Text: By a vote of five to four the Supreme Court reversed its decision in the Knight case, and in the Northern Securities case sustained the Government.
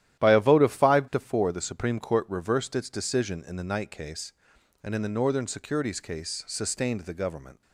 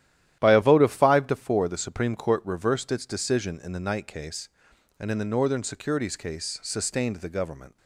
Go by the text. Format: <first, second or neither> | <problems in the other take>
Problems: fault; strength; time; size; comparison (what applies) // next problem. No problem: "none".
neither | starts louder than the rest; strong; the same in both